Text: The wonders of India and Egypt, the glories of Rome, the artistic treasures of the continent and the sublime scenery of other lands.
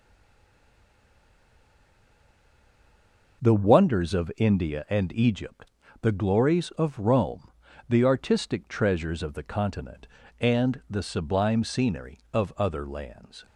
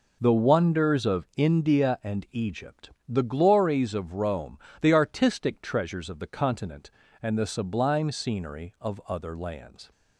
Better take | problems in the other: second | stays silent before the first word; strong; until 3.4 s; 3.4 s long

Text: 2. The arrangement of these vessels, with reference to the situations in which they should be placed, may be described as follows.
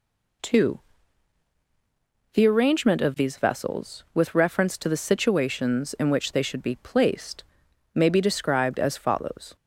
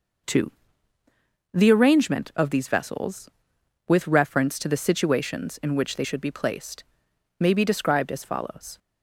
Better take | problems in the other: neither | none

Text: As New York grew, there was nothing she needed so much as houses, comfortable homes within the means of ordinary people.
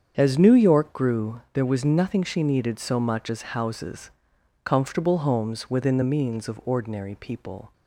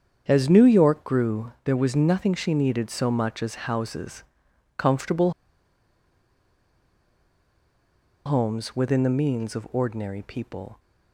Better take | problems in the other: first | starts louder than the rest; strong; until 1.2 s; 7.5 dB; strong in the first // pauses between "comfortable" and "homes"; strong; at 5.3 s; 2.9 s long

